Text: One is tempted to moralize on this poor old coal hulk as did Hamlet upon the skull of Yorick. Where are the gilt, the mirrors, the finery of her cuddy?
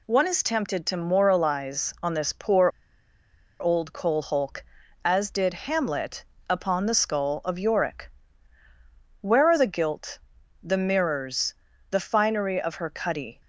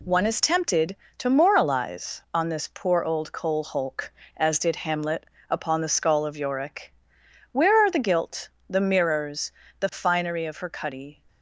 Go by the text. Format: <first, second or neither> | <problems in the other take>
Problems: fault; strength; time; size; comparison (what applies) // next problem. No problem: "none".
second | pauses between "poor" and "old"; noticeable; at 2.6 s; 0.90 s long // pauses between "Hamlet" and "upon"; slight; at 6.2 s; 0.28 s long; slight in the second